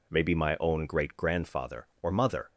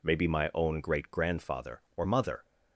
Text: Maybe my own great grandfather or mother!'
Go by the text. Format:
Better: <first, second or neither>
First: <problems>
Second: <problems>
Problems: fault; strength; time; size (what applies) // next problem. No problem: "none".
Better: neither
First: none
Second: none